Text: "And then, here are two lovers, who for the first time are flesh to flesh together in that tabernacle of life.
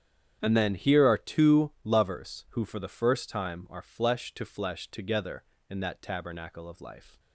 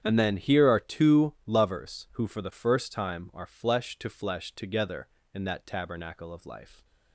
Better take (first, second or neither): neither